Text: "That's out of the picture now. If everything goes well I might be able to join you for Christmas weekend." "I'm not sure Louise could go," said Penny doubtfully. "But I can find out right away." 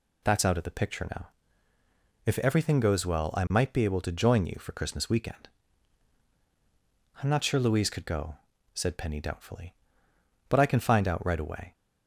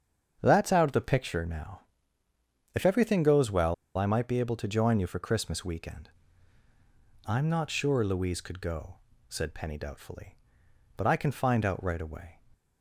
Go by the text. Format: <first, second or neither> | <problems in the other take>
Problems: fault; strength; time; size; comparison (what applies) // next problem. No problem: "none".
first | starts louder than the rest; strong; until 1.4 s; 7.5 dB // pauses between "well" and "I"; slight; at 3.7 s; 0.21 s long